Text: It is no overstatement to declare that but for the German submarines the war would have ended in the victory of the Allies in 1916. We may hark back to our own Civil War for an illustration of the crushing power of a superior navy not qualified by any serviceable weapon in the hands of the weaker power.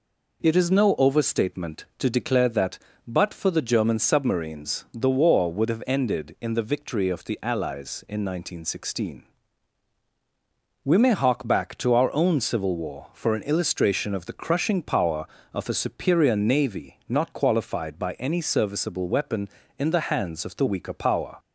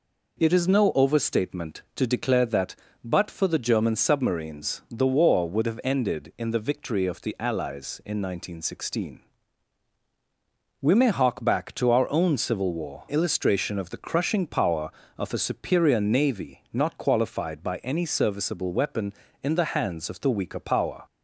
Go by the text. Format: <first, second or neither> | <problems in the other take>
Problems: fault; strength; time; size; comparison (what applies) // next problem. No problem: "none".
first | skips "for an"; at 13.0 s